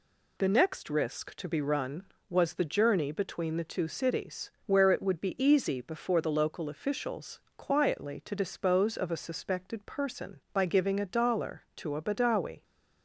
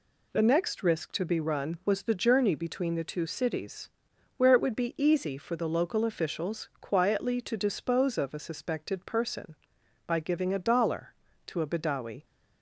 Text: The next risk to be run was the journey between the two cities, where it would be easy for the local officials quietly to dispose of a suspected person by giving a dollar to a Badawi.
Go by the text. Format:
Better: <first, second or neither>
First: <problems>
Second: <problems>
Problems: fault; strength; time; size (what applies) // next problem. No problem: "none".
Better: second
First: says "before" for "for"; at 5.8 s // pauses between "officials" and "quietly"; slight; at 7.3 s; 0.20 s long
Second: none